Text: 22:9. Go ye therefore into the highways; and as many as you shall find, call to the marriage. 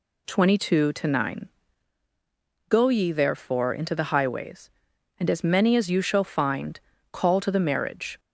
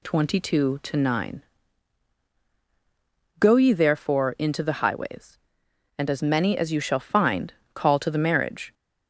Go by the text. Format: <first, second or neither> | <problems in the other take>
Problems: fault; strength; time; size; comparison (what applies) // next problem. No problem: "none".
neither | none